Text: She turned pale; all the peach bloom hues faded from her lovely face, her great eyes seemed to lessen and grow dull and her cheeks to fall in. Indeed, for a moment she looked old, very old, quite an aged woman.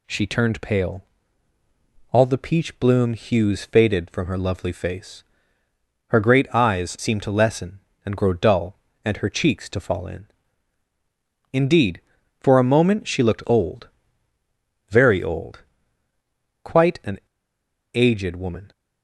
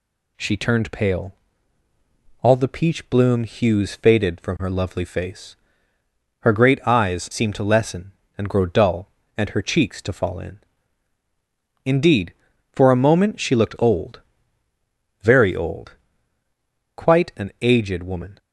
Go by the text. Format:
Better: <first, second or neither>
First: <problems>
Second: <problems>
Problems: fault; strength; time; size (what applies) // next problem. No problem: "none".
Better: second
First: pauses between "an" and "aged"; noticeable; at 17.1 s; 0.75 s long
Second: none